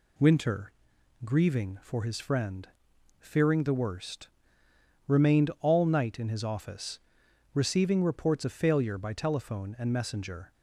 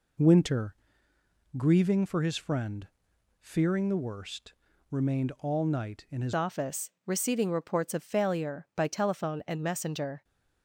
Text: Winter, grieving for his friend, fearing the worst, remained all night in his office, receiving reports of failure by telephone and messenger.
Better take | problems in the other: first | changes voice at "office"; from 6.3 s on; 3.9 s long

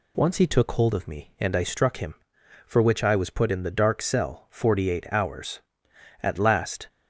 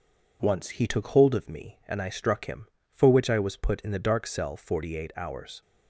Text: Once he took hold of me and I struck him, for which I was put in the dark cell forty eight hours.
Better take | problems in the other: second | goes on to say "At last"; noticeable; from 6.2 s on; 0.66 s long

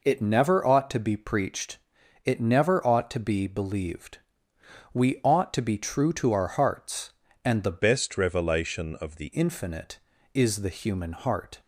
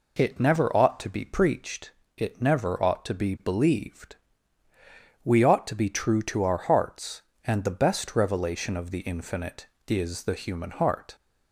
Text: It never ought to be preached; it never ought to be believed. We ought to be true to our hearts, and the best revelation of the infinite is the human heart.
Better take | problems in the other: second | changes voice from "best" to "the"; from 7.7 to 9.3 s; 1.6 s long

